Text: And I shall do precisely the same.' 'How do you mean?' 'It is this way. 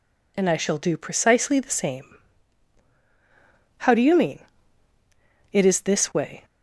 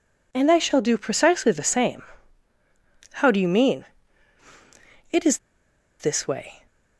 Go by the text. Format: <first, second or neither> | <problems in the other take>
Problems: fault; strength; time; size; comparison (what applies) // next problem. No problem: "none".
first | pauses between "is" and "this"; noticeable; at 5.3 s; 0.60 s long